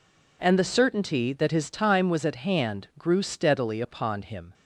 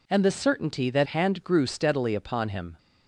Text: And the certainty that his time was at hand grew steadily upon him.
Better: first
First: none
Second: skips "his time was at"; at 1.0 s

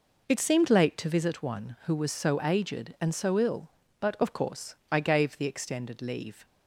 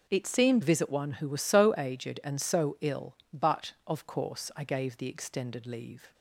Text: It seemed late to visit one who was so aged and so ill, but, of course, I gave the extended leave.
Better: first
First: none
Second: skips "late to"; at 0.6 s

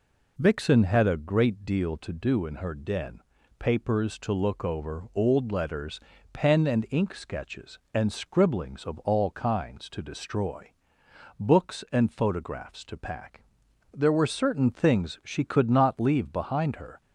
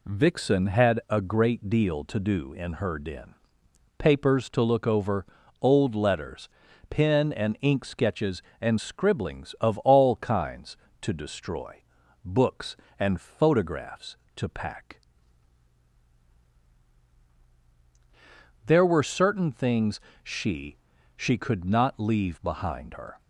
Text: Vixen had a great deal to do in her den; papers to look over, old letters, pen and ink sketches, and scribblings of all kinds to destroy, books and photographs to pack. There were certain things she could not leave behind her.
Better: first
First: none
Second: pauses between "things" and "she"; slight; at 20.0 s; 0.22 s long // says "she" twice; at 21.1 s

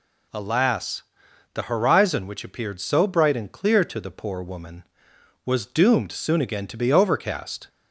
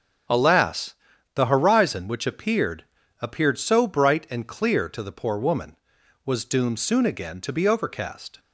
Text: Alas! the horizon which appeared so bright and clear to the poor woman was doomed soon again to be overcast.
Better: first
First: none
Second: starts louder than the rest; strong; until 1.7 s; 7.5 dB // says "appeared" twice; at 3.2 s

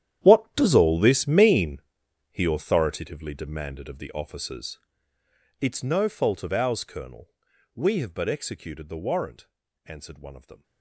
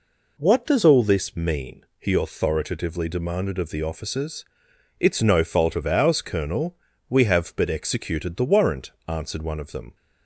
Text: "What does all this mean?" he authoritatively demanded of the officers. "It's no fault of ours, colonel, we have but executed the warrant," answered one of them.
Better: second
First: gets quieter; strong; throughout; 15 dB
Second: none

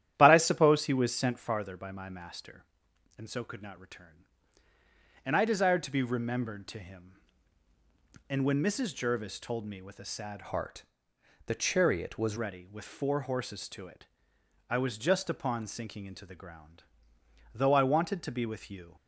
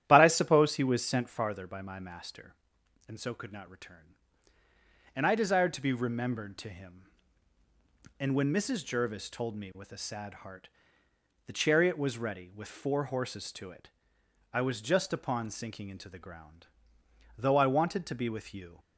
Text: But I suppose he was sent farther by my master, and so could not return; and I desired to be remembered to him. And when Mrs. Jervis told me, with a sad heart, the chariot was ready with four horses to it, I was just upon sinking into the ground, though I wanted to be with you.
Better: second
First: starts louder than the rest; strong; until 1.1 s; 11.5 dB // changes voice from "heart" to "was"; from 10.4 to 12.3 s; 1.9 s long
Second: starts louder than the rest; strong; until 1.0 s; 11.5 dB

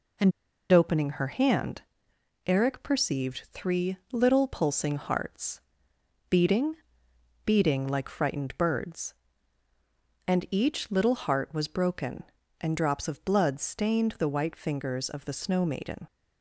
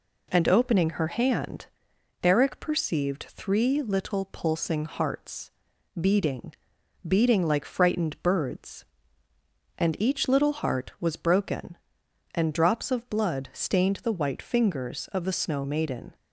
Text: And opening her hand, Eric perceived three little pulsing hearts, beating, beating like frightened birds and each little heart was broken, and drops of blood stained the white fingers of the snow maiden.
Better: second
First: pauses between "And" and "opening"; at 0.3 s; 0.40 s long // pauses between "three" and "little"; slight; at 3.9 s; 0.16 s long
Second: none

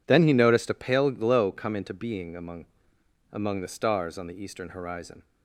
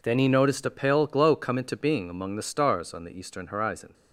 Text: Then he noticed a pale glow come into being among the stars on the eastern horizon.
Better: second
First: says "among" twice; at 3.3 s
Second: none

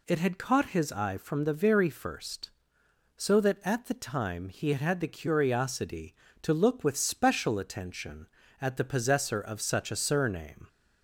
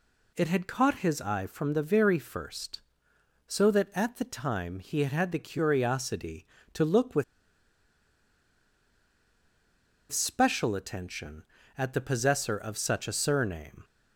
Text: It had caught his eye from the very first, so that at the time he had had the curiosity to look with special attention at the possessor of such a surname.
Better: first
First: none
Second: pauses between "with" and "special"; strong; at 7.2 s; 2.8 s long

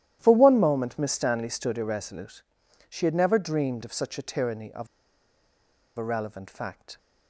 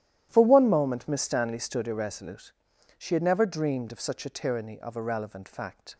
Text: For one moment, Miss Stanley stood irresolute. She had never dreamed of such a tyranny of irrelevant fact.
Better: second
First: starts louder than the rest; strong; until 1.2 s; 12.5 dB // pauses between "of" and "irrelevant"; at 4.8 s; 1.1 s long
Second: starts louder than the rest; strong; until 1.3 s; 12.5 dB

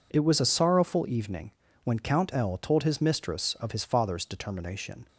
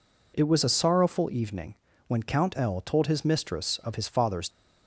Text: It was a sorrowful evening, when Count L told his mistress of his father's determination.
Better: first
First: none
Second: stops before "determination"; at 4.4 s

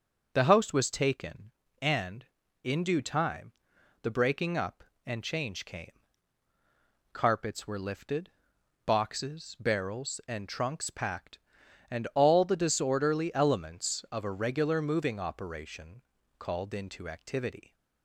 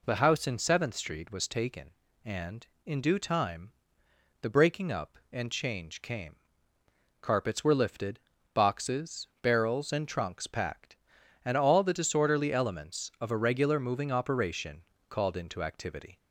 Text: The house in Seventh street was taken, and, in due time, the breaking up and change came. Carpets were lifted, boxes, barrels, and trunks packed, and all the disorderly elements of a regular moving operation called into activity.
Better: second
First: starts louder than the rest; until 1.3 s; 6.5 dB // skips "in Seventh street"; at 0.7 s // pauses between "operation" and "called"; slight; at 16.0 s; 0.36 s long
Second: pauses between "operation" and "called"; slight; at 14.8 s; 0.26 s long

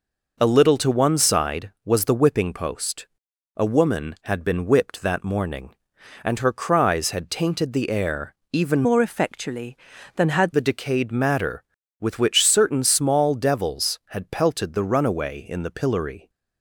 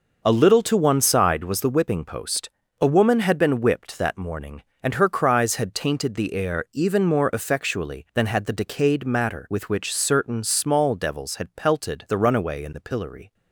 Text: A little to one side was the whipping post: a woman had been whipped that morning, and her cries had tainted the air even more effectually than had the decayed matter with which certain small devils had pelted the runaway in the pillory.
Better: second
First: pauses between "air" and "even"; slight; at 8.3 s; 0.16 s long // changes voice from "more" to "had"; from 8.8 to 10.5 s; 1.7 s long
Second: none

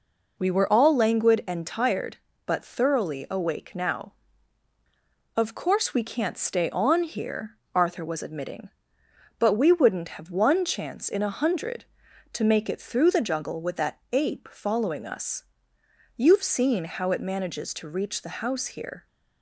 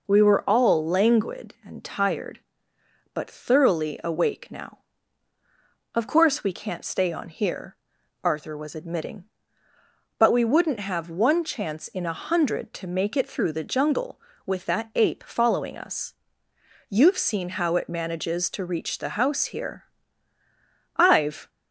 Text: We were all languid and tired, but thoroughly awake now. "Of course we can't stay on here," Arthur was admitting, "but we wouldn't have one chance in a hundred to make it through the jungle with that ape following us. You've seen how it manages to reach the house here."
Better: first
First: none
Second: goes on to say "I've"; from 20.9 s on; 0.54 s long

